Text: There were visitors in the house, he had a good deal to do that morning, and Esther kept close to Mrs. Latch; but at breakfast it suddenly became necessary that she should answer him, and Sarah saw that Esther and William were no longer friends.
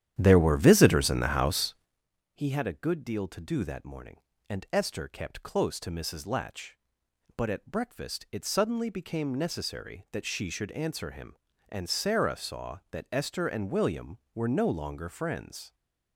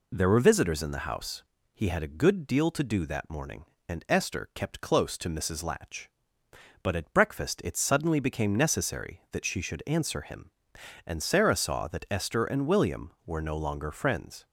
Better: second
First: starts louder than the rest; strong; until 2.0 s; 10.5 dB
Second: none

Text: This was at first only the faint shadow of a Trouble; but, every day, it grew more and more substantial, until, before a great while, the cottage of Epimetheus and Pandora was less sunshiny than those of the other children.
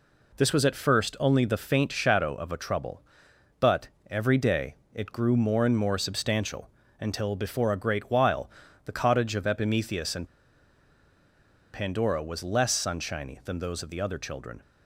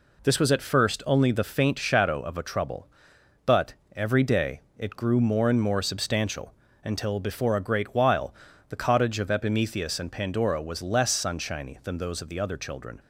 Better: second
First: pauses between "and" and "Pandora"; strong; at 10.2 s; 1.4 s long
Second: none

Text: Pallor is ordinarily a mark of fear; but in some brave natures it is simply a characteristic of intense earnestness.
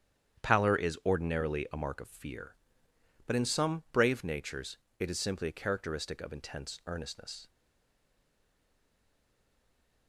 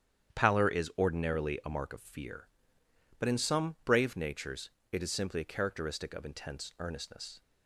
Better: second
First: starts louder than the rest; strong; until 1.4 s; 9.5 dB // pauses between "natures" and "it"; slight; at 4.7 s; 0.22 s long // stays silent after the last word; strong; from 7.4 s on; 2.6 s long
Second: starts louder than the rest; strong; until 1.4 s; 9.5 dB // pauses between "natures" and "it"; slight; at 4.6 s; 0.22 s long

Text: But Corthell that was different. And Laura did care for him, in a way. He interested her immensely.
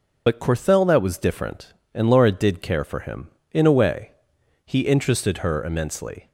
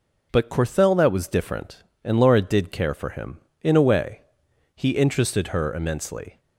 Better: second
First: loses the start of "But"; at 0.2 s; 50 ms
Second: none

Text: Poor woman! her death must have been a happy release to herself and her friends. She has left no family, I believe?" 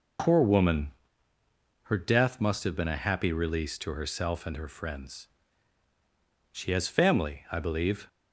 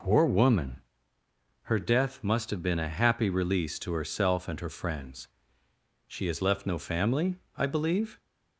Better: second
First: skips "left no"; at 6.8 s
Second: none

